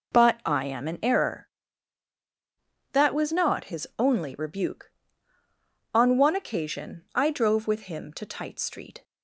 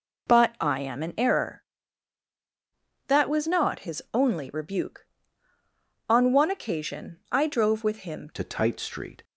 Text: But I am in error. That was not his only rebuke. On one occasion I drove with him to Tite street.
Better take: first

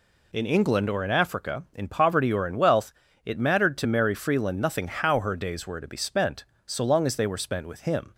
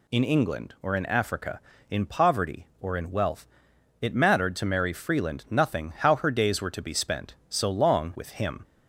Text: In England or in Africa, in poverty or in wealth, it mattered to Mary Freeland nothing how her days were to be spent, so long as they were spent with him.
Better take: first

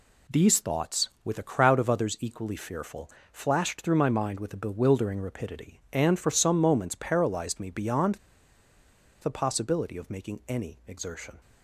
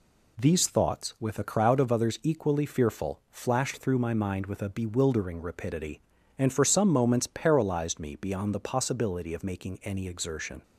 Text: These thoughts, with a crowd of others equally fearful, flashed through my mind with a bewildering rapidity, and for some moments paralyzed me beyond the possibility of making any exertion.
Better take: second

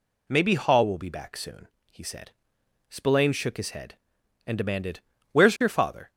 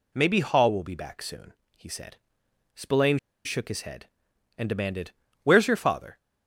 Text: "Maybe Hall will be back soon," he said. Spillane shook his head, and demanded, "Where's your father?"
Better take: first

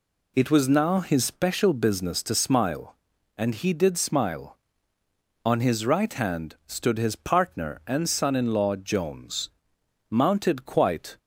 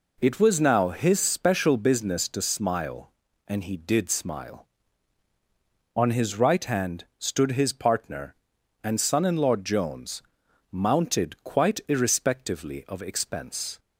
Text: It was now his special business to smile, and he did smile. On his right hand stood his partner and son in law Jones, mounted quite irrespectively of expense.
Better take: second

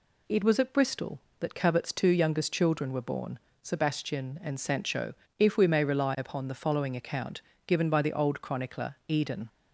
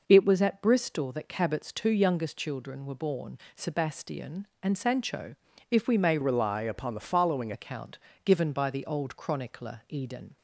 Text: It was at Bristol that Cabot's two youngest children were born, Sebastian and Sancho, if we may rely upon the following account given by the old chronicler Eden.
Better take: first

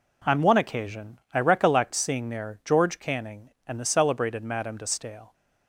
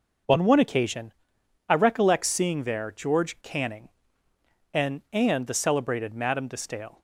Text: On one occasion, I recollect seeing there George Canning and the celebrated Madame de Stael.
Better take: first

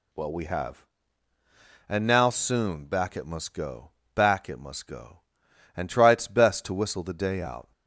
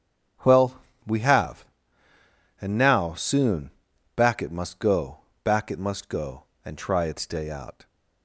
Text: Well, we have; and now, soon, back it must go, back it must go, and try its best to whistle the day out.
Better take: first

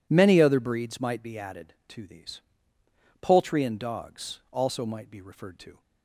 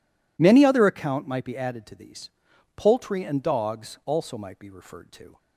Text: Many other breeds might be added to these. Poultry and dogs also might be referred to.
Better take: first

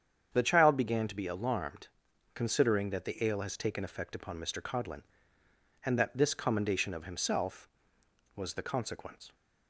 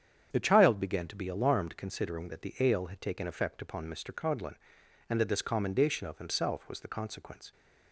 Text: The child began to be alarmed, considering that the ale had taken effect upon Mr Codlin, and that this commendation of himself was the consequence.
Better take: second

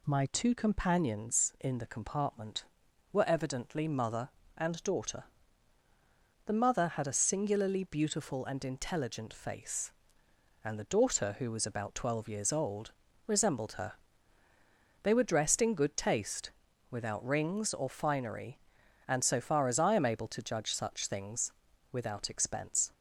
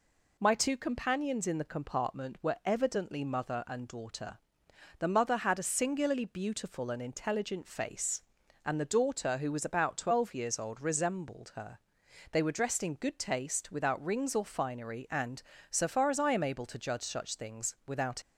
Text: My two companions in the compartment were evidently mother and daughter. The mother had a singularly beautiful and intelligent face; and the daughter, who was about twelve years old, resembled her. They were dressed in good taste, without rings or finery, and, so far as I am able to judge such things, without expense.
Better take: first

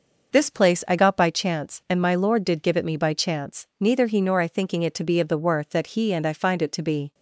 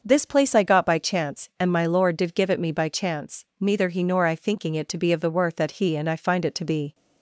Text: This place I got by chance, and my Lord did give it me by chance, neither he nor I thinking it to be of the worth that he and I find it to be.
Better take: neither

